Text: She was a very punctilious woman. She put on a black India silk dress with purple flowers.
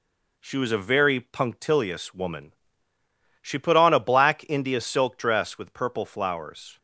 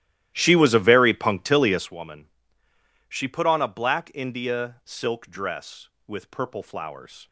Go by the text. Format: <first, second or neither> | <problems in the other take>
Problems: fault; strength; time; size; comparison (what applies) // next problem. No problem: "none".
first | starts louder than the rest; strong; until 1.9 s; 14 dB